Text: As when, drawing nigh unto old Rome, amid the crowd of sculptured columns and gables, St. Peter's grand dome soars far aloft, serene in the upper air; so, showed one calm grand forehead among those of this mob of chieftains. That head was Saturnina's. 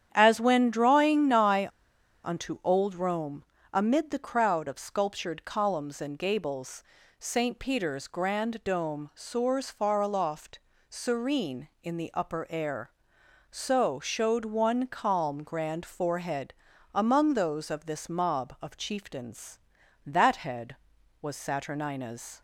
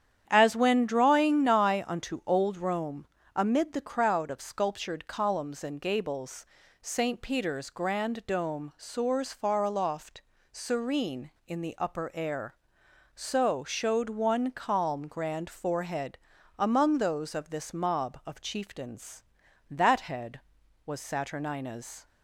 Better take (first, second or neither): second